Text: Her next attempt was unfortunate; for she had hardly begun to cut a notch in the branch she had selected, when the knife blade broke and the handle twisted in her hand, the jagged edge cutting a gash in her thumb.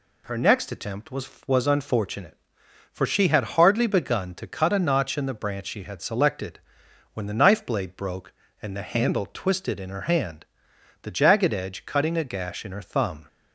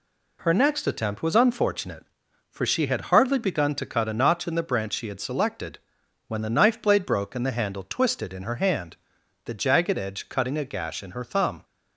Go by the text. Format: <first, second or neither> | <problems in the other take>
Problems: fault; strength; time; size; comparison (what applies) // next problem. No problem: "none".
second | says "was" twice; at 1.4 s